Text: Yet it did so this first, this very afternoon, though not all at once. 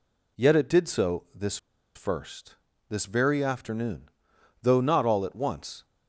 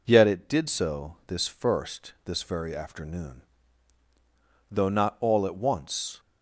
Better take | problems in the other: second | pauses between "this" and "first"; at 1.5 s; 0.38 s long

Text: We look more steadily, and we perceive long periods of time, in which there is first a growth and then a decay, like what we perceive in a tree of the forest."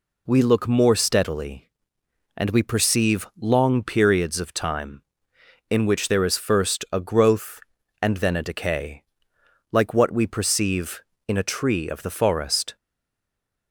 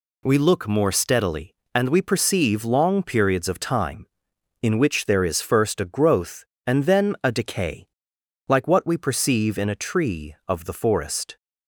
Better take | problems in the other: second | stays silent after the last word; slight; from 12.7 s on; 1.0 s long

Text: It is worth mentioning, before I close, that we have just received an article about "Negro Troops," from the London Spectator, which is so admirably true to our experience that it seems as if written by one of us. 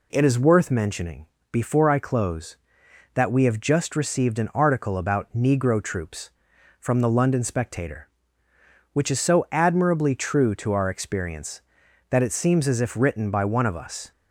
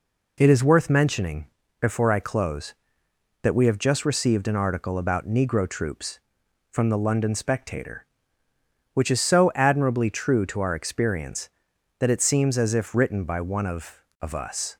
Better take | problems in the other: first | says "of" twice; at 14.2 s

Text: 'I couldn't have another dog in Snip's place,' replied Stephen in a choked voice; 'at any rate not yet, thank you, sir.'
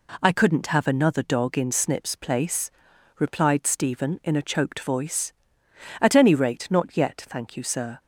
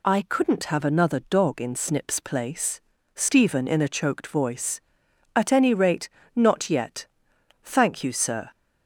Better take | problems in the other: first | skips "replied"; at 2.9 s // pauses between "rate" and "not"; slight; at 6.0 s; 0.28 s long

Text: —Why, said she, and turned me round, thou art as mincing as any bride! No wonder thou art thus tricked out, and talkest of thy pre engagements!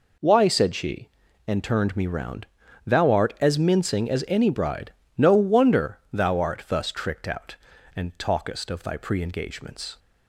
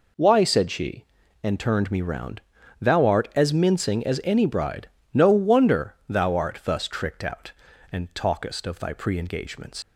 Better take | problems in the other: first | leaves "engagements" unfinished; at 9.8 s; 125 ms

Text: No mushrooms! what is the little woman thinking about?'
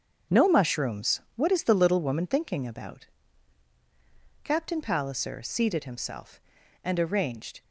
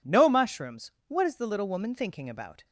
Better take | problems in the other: second | starts louder than the rest; until 1.4 s; 6.5 dB // goes on to say "Captain Palliser seated himself and arranged"; strong; from 4.4 s on; 3.1 s long

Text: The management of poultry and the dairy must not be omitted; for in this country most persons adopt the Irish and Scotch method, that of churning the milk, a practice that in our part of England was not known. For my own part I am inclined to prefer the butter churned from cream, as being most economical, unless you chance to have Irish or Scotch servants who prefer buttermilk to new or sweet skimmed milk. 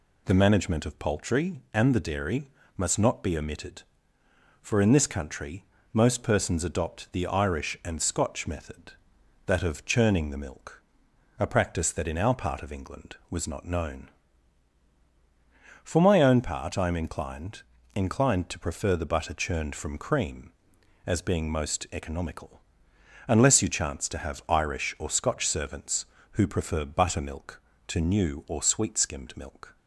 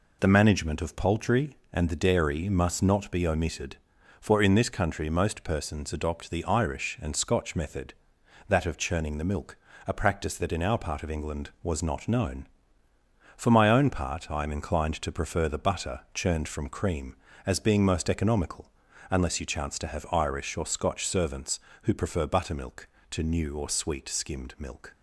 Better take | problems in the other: second | pauses between "dairy" and "must"; slight; at 2.4 s; 0.30 s long // pauses between "country" and "most"; slight; at 5.6 s; 0.26 s long // says "inclined" twice; at 17.9 s

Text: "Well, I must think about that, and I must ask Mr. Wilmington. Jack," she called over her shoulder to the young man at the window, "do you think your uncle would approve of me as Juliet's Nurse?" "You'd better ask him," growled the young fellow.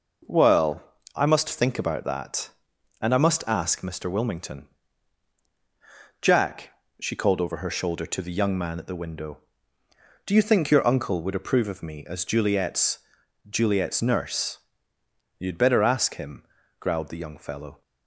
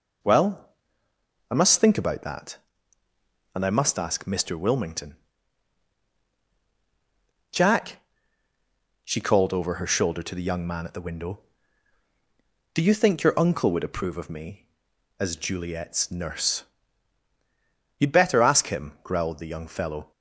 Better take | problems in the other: second | says "Juliet's" twice; at 13.4 s

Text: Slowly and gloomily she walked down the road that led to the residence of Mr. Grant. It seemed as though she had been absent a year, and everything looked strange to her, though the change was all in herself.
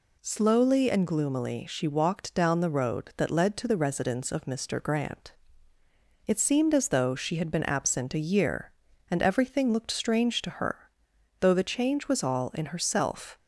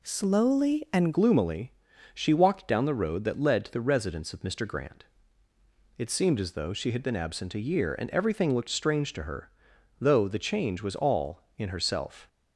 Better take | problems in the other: first | changes voice at "gloomily"; from 1.1 s on; 11.1 s long // pauses between "gloomily" and "she"; at 1.7 s; 0.42 s long

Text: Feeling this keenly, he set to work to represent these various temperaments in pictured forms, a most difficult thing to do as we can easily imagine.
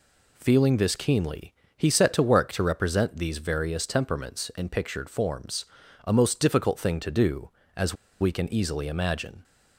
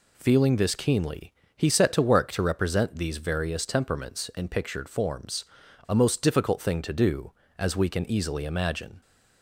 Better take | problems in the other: second | pauses between "as" and "we"; slight; at 7.9 s; 0.26 s long

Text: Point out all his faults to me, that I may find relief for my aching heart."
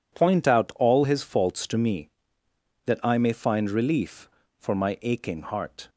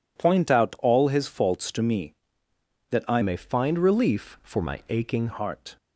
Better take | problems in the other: first | changes voice from "may" to "aching"; from 3.2 to 5.2 s; 2.0 s long

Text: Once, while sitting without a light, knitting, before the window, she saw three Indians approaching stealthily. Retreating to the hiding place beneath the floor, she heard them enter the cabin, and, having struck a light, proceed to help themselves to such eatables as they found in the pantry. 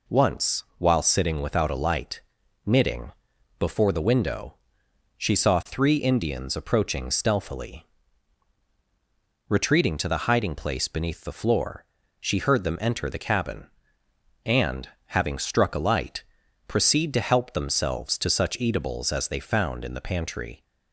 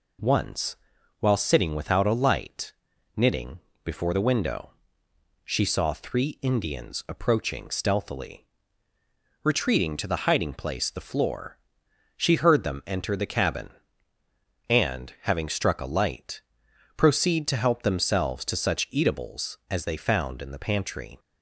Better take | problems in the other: first | skips "beneath"; at 10.8 s

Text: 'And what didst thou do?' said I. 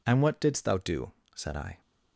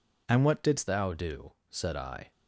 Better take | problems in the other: first | changes voice at "thou"; from 0.8 s on; 1.5 s long

